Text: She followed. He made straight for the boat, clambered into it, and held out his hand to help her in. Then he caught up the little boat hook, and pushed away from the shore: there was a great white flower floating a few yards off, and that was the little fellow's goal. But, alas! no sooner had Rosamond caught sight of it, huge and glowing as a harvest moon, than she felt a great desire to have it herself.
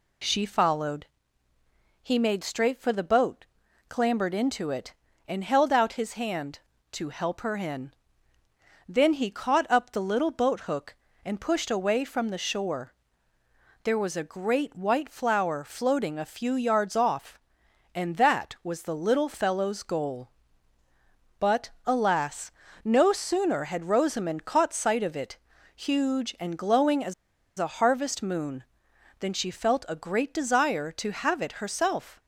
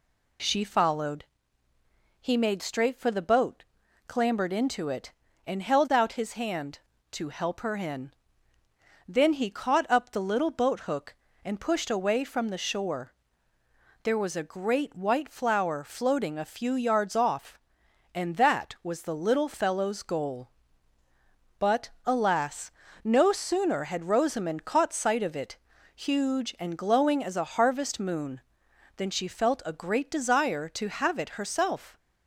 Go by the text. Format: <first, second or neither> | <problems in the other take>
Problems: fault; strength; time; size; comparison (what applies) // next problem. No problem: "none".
second | pauses between "as" and "a"; at 27.1 s; 0.45 s long